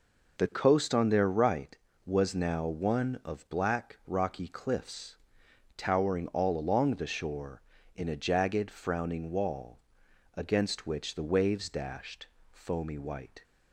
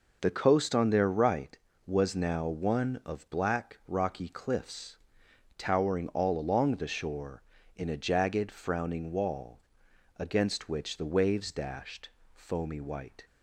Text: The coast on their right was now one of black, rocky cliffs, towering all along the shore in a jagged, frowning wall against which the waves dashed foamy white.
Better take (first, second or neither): neither